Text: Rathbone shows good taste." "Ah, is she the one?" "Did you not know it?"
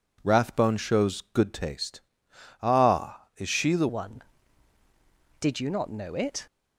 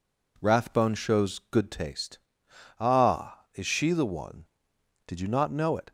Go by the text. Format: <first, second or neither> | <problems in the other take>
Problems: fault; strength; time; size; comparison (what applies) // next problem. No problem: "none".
second | changes voice at "one"; from 3.8 s on; 2.6 s long